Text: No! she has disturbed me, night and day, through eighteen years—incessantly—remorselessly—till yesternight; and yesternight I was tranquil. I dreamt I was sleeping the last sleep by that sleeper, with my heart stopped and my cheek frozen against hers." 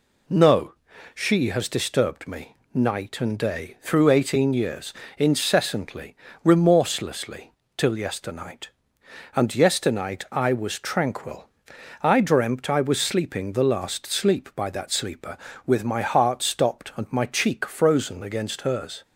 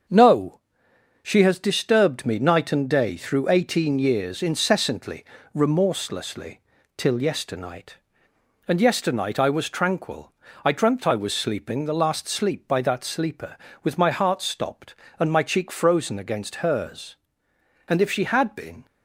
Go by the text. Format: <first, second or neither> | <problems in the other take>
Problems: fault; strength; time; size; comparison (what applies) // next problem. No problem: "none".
first | starts louder than the rest; until 1.6 s; 6.5 dB // goes on to say "And if she had been"; noticeable; from 17.8 s on; 0.96 s long